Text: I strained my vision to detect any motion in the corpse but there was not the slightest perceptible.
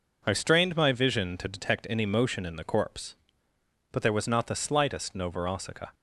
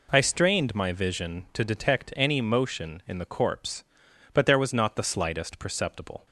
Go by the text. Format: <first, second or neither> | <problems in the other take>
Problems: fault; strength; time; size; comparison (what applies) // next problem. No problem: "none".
second | says "novorossica" for "perceptible"; at 5.1 s